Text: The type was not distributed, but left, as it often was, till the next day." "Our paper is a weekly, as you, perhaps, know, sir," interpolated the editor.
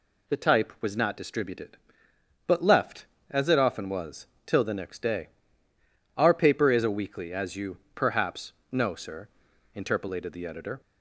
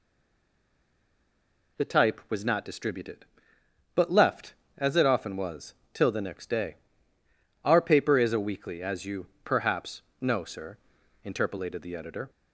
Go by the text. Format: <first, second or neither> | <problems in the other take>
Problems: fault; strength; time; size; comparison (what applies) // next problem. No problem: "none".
first | stays silent before the first word; noticeable; until 1.7 s; 1.7 s long